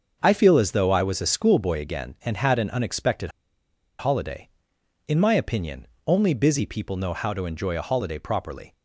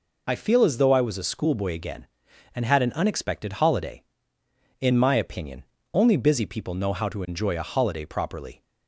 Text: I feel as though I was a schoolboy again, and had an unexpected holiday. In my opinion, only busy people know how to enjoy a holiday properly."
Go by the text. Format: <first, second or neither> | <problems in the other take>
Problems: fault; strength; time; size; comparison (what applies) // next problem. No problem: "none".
second | starts louder than the rest; until 1.2 s; 6.5 dB // pauses between "unexpected" and "holiday"; noticeable; at 3.3 s; 0.68 s long